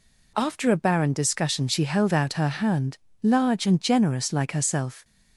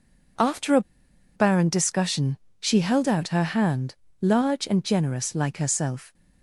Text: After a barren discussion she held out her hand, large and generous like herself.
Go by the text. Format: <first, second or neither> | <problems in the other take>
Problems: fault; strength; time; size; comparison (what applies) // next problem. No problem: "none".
first | pauses between "a" and "barren"; noticeable; at 0.8 s; 0.53 s long // pauses between "discussion" and "she"; slight; at 2.3 s; 0.24 s long